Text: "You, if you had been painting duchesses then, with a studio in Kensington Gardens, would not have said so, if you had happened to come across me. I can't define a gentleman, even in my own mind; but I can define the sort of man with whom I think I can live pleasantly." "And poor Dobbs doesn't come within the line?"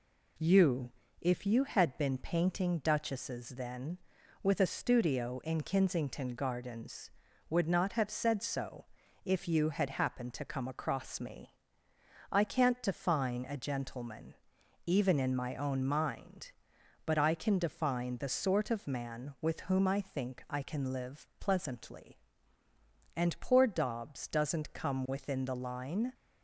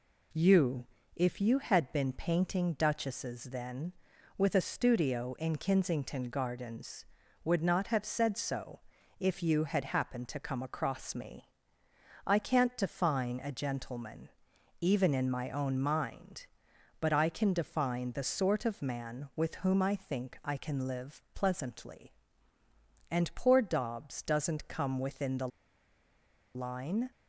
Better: first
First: none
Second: pauses between "the" and "line"; at 25.4 s; 1.0 s long

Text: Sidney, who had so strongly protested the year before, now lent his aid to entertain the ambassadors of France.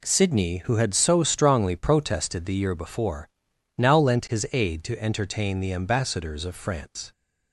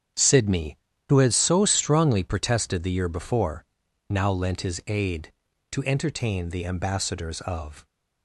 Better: first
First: none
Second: starts louder than the rest; strong; until 1.4 s; 8.5 dB // stops before "France"; at 7.8 s

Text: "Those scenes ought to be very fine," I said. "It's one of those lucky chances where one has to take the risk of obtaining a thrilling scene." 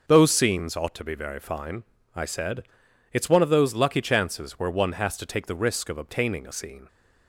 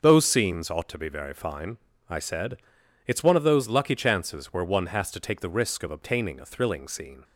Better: second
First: starts louder than the rest; noticeable; until 1.0 s; 6 dB // skips "thrilling"; at 6.5 s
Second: starts louder than the rest; until 1.0 s; 6.5 dB

